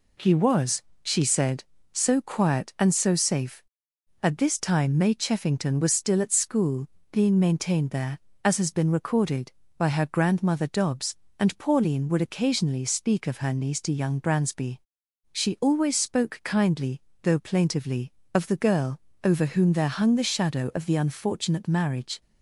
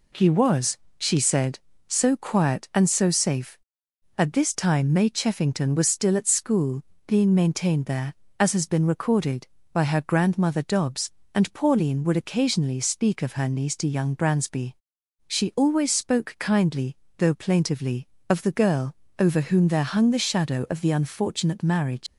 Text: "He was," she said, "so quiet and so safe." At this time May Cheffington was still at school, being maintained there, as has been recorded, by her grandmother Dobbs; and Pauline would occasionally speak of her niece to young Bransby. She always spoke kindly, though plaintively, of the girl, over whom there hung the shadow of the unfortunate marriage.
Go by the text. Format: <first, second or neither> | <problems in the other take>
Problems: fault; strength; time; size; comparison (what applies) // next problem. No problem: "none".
first | leaves "marriage" unfinished; at 22.0 s; 90 ms